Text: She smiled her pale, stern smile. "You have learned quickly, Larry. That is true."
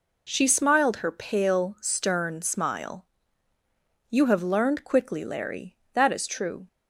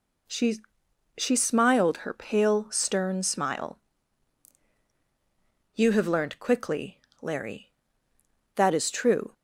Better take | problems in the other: first | says "She" twice; at 1.1 s

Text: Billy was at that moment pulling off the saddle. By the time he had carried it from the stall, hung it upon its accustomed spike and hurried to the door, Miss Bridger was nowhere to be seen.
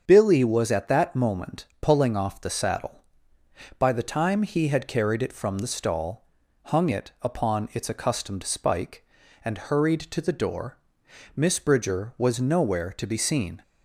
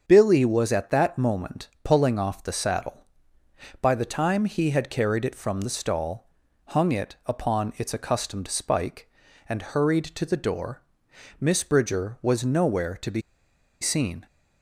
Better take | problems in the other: first | starts louder than the rest; until 1.0 s; 7 dB; also in the first // pauses between "moment" and "pulling"; slight; at 1.6 s; 0.16 s long; slight in the first // pauses between "be" and "seen"; noticeable; at 13.2 s; 0.60 s long

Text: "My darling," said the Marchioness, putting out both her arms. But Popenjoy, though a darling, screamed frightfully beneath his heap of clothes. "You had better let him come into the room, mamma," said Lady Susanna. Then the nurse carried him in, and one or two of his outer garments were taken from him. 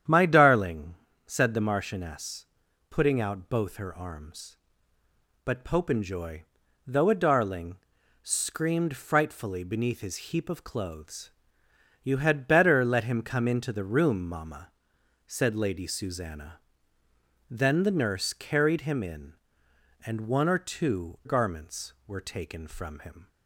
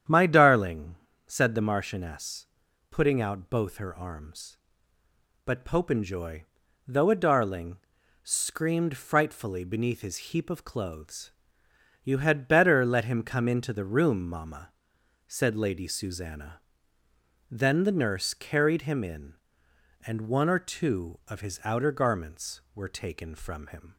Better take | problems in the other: second | starts louder than the rest; strong; until 1.4 s; 9.5 dB; strong in the second // skips "of his outer"; at 21.2 s

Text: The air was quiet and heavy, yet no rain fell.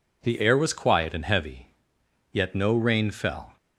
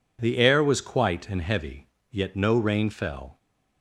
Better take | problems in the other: first | says "quite" for "quiet"; at 0.8 s

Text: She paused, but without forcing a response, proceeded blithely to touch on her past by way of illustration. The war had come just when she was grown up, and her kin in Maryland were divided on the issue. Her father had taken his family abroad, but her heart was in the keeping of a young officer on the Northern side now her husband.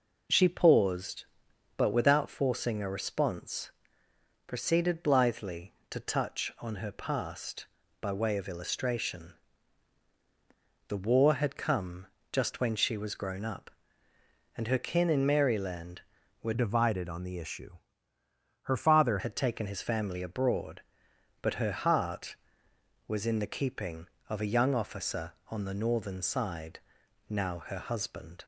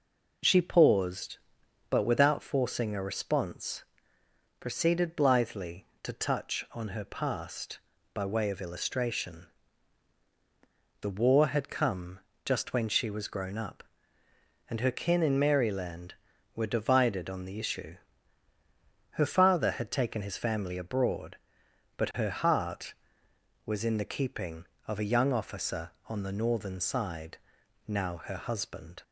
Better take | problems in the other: second | pauses between "come" and "just"; slight; at 12.0 s; 0.24 s long; slight in the second // changes voice from "divided" to "father"; from 16.5 to 19.1 s; 2.6 s long // pauses between "side" and "now"; noticeable; at 26.7 s; 0.50 s long; noticeable in the second

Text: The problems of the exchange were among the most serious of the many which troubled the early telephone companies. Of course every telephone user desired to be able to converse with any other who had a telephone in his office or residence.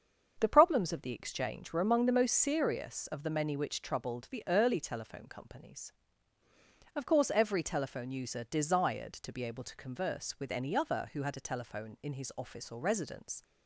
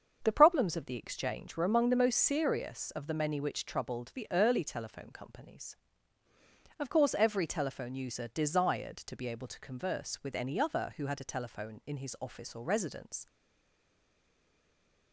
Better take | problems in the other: first | starts louder than the rest; until 1.2 s; 7 dB; strong in the first // stays silent after the last word; noticeable; from 13.2 s on; 1.9 s long

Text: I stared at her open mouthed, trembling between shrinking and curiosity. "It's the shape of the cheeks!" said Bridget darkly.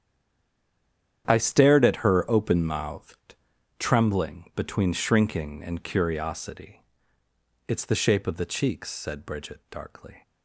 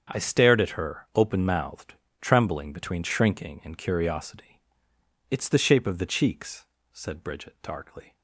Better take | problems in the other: second | stays silent before the first word; noticeable; until 1.2 s; 1.2 s long // starts louder than the rest; strong; until 2.2 s; 9 dB; strong in the second

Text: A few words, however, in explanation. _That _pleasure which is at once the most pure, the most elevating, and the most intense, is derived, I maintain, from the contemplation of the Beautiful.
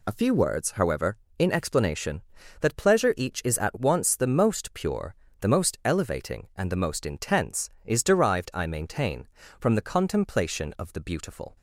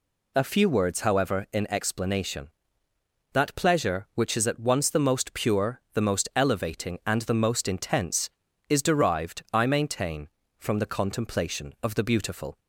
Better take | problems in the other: second | says "each" for "which"; at 3.1 s

